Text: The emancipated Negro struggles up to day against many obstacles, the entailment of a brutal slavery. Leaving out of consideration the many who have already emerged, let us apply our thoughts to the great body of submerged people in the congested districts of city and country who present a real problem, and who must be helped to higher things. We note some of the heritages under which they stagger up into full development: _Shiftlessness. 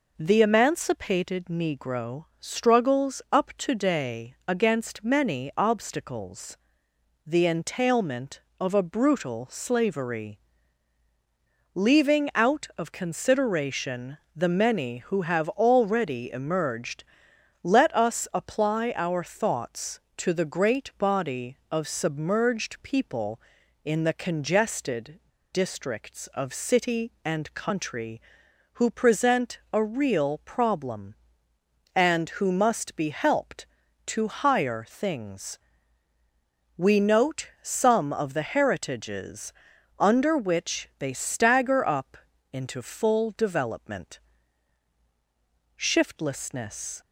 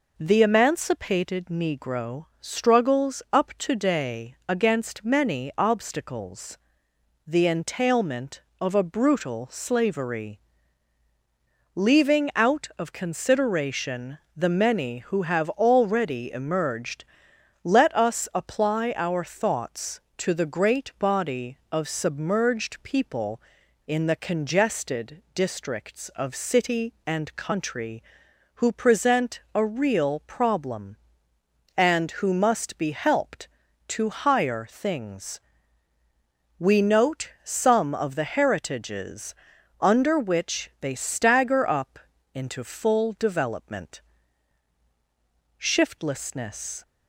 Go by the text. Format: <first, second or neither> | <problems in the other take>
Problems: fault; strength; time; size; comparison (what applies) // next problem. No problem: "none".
second | pauses between "Negro" and "struggles"; slight; at 2.2 s; 0.16 s long; slight in the second // pauses between "consideration" and "the"; slight; at 14.1 s; 0.18 s long; slight in the second // pauses between "congested" and "districts"; slight; at 25.1 s; 0.34 s long // pauses between "heritages" and "under"; at 39.5 s; 0.44 s long; also in the second // pauses between "up" and "into"; slight; at 42.1 s; 0.34 s long; slight in the second